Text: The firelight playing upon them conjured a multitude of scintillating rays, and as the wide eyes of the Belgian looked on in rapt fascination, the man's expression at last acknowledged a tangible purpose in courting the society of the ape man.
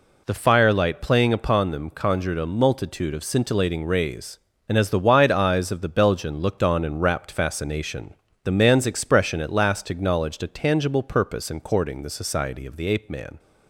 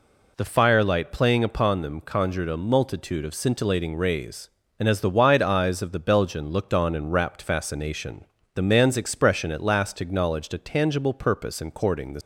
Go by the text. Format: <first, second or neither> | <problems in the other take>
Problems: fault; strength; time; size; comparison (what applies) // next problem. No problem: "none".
first | stops before "society of the ape man"; at 12.2 s